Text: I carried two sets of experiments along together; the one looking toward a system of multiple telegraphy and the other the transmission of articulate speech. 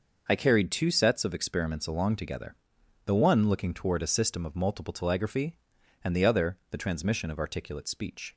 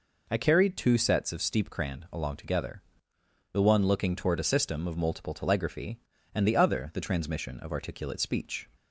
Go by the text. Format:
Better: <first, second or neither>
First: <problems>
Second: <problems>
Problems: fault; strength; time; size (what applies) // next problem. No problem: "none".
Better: first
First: none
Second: says "steepcrand" for "experiments"; at 1.4 s